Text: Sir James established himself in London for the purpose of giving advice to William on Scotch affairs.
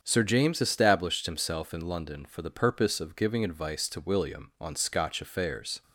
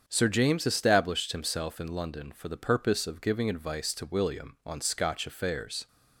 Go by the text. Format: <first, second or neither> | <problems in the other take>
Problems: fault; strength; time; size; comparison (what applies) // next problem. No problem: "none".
neither | starts louder than the rest; strong; the same in both